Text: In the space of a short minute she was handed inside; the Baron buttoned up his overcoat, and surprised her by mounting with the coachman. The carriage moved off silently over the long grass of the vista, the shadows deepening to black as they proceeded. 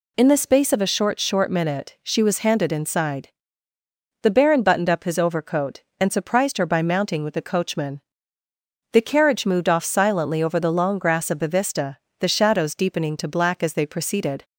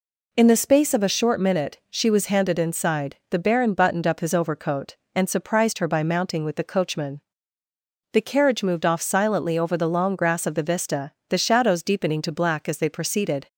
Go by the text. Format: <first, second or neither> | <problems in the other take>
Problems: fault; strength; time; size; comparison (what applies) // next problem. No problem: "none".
second | says "short" twice; at 1.1 s